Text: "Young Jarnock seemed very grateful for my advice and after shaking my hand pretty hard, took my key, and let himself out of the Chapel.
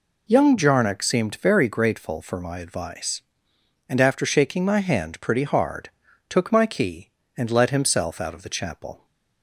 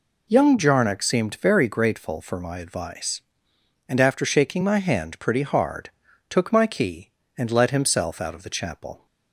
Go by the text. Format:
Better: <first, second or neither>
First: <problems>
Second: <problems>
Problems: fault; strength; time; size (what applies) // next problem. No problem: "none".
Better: neither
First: none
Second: none